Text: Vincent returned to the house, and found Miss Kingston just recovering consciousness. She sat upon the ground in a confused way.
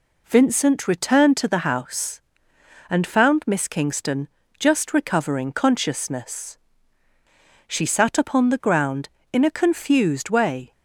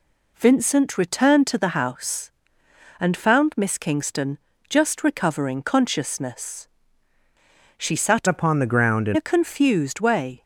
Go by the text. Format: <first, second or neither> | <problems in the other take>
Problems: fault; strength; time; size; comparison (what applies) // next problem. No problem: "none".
first | pauses between "Kingston" and "just"; slight; at 4.3 s; 0.30 s long; slight in the first // changes voice from "upon" to "in"; from 8.2 to 9.1 s; 0.9 s long